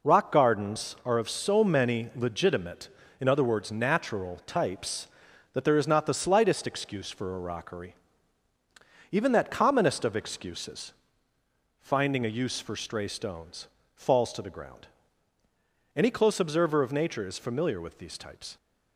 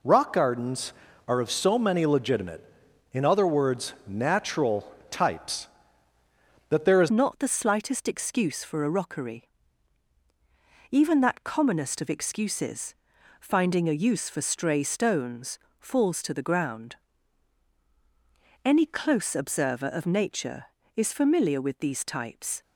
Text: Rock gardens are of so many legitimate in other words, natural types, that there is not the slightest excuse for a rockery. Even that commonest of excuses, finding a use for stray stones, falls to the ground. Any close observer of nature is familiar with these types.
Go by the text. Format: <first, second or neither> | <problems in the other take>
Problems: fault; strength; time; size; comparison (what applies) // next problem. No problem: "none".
first | pauses between "natural" and "types"; slight; at 4.8 s; 0.24 s long // changes voice at "not"; from 7.0 s on; 15.6 s long